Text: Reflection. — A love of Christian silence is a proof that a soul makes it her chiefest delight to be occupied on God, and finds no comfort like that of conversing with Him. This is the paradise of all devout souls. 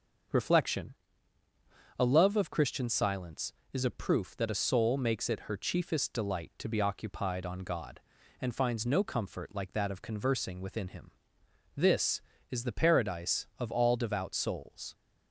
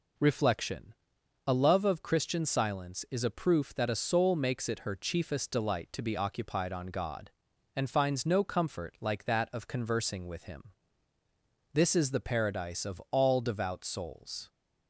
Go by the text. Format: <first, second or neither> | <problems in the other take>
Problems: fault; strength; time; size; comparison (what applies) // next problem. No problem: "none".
second | starts louder than the rest; until 2.3 s; 6.5 dB // says "within" for "with"; at 10.6 s